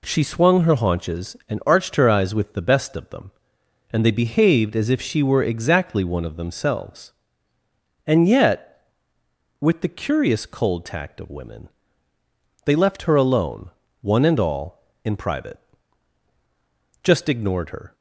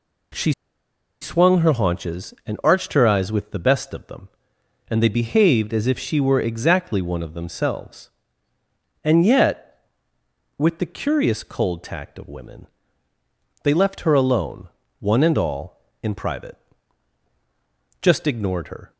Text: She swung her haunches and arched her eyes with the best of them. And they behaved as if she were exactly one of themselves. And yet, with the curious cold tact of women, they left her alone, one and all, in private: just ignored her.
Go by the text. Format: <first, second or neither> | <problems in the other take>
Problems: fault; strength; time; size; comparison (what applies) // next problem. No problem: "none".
first | pauses between "She" and "swung"; noticeable; at 0.5 s; 0.70 s long